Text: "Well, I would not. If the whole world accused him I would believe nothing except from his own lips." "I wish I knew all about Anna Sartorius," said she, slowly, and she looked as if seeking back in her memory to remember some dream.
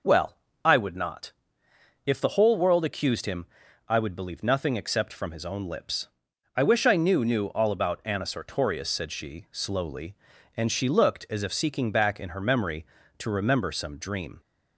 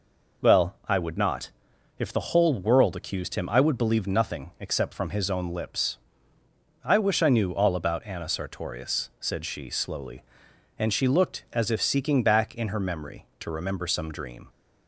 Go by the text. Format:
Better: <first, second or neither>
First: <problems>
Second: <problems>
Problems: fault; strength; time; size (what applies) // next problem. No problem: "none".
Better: second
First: pauses between "him" and "I"; at 3.4 s; 0.42 s long // says "knew" twice; at 7.2 s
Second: none